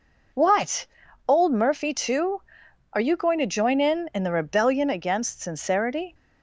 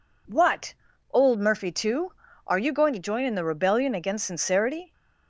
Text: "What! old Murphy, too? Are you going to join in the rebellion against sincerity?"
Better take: second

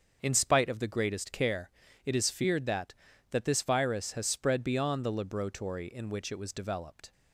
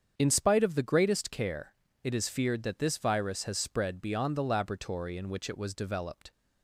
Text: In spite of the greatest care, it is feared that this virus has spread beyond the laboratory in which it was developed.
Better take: second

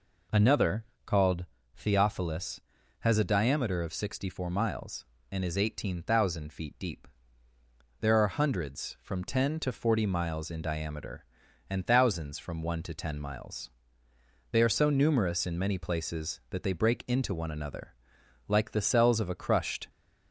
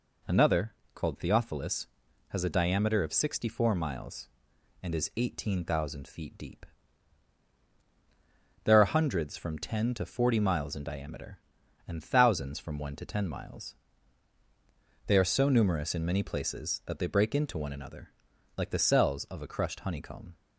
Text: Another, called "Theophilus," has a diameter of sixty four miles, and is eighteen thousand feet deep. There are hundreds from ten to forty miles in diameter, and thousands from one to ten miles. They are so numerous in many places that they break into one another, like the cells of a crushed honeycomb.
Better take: second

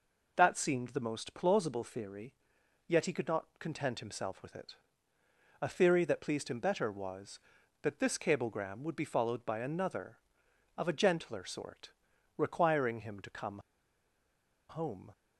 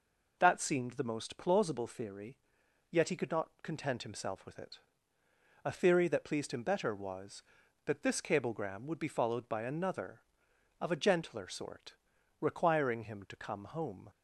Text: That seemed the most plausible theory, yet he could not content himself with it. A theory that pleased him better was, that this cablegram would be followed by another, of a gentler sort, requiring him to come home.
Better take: second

